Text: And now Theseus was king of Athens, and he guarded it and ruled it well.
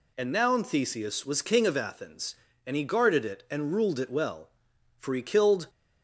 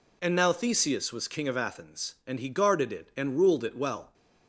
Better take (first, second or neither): second